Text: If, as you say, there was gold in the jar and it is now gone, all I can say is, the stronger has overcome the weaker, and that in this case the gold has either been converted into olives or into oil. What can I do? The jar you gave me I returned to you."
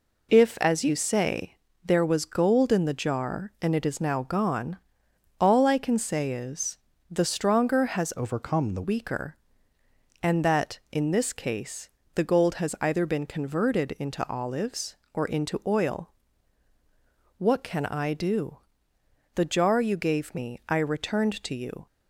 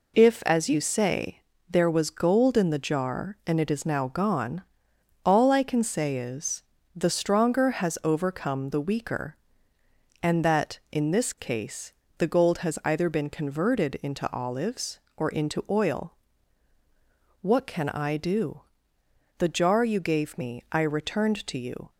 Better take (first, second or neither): second